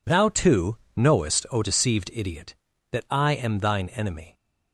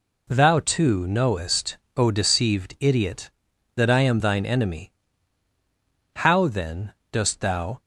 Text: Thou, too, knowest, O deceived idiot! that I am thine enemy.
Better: first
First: none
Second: goes on to say "How then dost thou"; from 6.1 s on; 1.6 s long

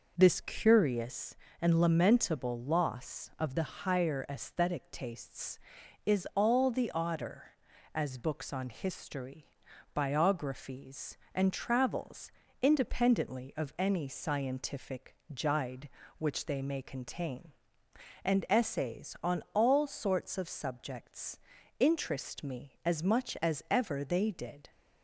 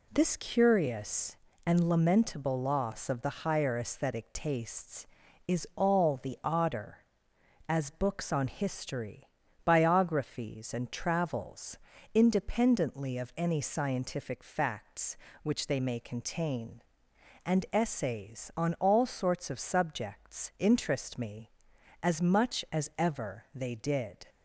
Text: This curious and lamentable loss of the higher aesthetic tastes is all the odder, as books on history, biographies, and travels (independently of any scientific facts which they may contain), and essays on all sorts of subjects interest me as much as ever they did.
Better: second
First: says "jide" for "facts"; at 15.3 s // pauses between "subjects" and "interest"; at 21.3 s; 0.42 s long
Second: none

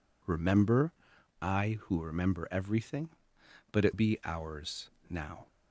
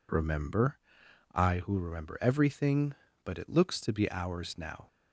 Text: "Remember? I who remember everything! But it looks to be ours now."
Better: second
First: skips "looks to"; at 3.9 s // pauses between "ours" and "now"; slight; at 4.8 s; 0.20 s long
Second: none

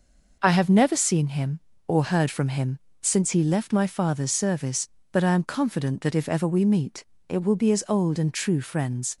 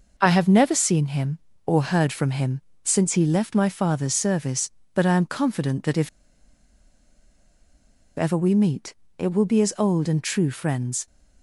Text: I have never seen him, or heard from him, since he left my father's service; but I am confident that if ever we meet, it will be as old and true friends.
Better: first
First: none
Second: pauses between "if" and "ever"; strong; at 6.0 s; 2.0 s long

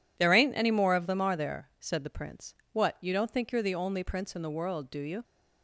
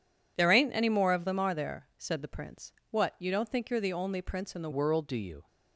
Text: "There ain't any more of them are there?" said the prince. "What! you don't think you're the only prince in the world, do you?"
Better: first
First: none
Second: changes voice at "world"; from 4.7 s on; 0.7 s long

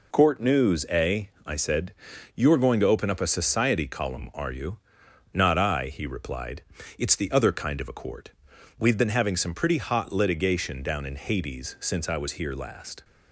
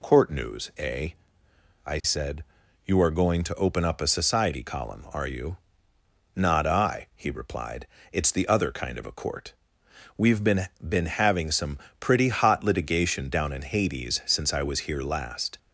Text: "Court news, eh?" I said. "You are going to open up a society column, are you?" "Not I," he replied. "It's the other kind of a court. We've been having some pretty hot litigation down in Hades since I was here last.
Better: first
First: none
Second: says "been" twice; at 10.7 s // pauses between "some" and "pretty"; slight; at 11.7 s; 0.20 s long

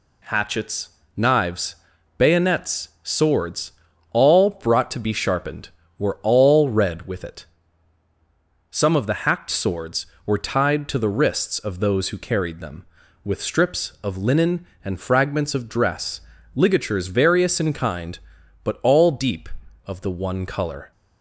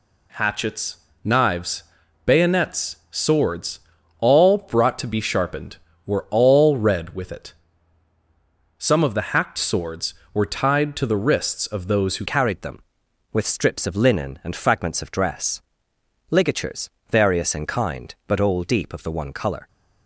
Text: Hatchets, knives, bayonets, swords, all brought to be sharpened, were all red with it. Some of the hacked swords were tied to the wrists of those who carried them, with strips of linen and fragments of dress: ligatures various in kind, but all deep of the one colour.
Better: first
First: none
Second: changes voice at "carried"; from 12.2 s on; 7.4 s long // pauses between "ligatures" and "various"; slight; at 16.8 s; 0.24 s long

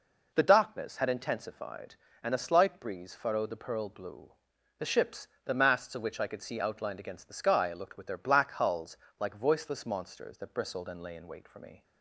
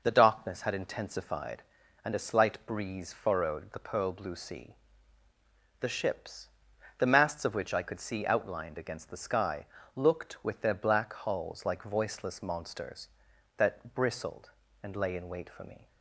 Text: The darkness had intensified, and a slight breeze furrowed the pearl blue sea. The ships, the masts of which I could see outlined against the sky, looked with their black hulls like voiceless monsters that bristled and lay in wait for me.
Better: second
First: skips "sea"; at 4.5 s // pauses between "hulls" and "like"; slight; at 8.9 s; 0.22 s long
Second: none

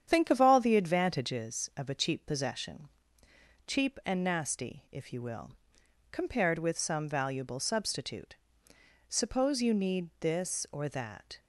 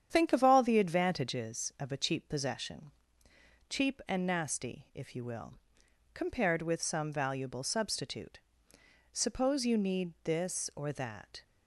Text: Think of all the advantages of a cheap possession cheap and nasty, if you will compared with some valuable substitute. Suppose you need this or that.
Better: neither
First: starts louder than the rest; strong; until 1.0 s; 9 dB // pauses between "possession" and "cheap"; noticeable; at 2.8 s; 0.78 s long // pauses between "will" and "compared"; noticeable; at 5.5 s; 0.60 s long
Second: starts louder than the rest; strong; until 1.1 s; 9 dB // pauses between "possession" and "cheap"; noticeable; at 2.9 s; 0.78 s long // pauses between "will" and "compared"; noticeable; at 5.5 s; 0.60 s long

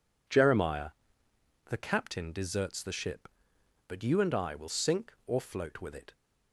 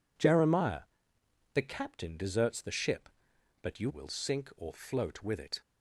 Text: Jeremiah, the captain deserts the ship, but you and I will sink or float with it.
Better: first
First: none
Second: skips "and I"; at 3.9 s

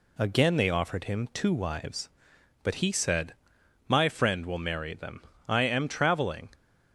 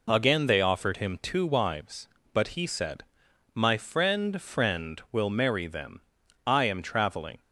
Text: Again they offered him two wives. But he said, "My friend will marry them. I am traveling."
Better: first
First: none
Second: says "friend" twice; at 4.3 s

